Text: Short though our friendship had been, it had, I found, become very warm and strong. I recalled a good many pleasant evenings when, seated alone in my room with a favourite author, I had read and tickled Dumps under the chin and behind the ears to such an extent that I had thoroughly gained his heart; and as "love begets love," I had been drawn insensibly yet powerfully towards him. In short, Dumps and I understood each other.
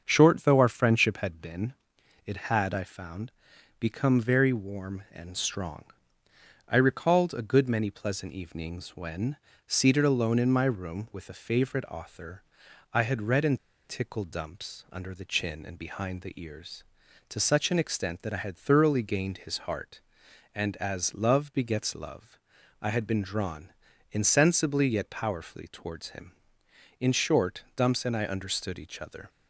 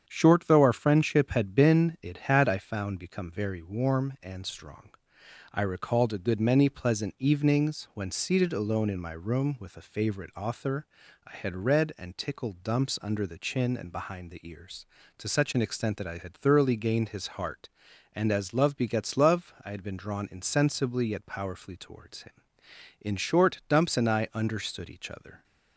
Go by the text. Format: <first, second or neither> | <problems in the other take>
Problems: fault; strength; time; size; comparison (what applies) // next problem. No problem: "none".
second | starts louder than the rest; until 1.0 s; 7 dB; strong in the second // pauses between "and" and "tickled"; slight; at 13.5 s; 0.29 s long // pauses between "drawn" and "insensibly"; at 23.7 s; 0.40 s long